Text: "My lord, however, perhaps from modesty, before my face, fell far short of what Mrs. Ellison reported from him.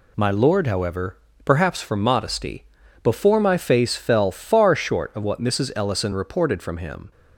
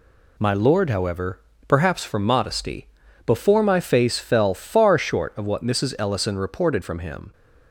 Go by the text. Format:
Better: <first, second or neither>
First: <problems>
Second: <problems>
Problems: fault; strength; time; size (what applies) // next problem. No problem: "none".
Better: neither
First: none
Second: none